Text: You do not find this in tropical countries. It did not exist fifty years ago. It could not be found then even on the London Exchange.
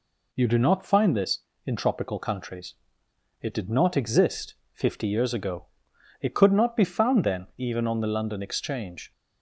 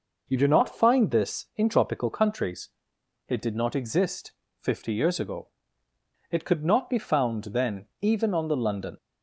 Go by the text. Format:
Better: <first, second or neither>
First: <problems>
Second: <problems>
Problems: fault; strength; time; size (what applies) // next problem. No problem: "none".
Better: first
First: pauses between "exist" and "fifty"; slight; at 4.5 s; 0.20 s long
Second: pauses between "exist" and "fifty"; slight; at 4.3 s; 0.26 s long // pauses between "then" and "even"; slight; at 7.8 s; 0.16 s long // stops before "Exchange"; at 8.9 s